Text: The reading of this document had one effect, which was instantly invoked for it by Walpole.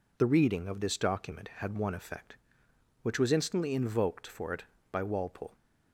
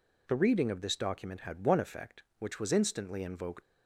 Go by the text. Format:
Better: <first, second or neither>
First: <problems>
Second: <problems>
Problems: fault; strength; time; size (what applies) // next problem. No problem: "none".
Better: first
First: none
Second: stops before "for it by Walpole"; at 3.6 s